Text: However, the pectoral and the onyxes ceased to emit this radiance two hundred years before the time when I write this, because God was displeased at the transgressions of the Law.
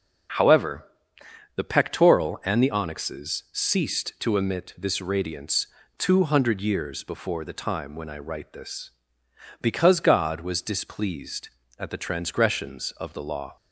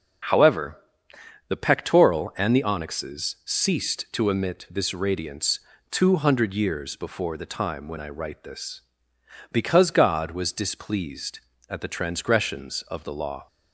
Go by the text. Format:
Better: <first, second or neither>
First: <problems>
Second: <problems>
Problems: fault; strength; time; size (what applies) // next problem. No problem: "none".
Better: neither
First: starts louder than the rest; until 2.0 s; 6.5 dB // pauses between "radiance" and "two"; slight; at 5.6 s; 0.32 s long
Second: starts louder than the rest; until 2.0 s; 6 dB // pauses between "radiance" and "two"; slight; at 5.5 s; 0.32 s long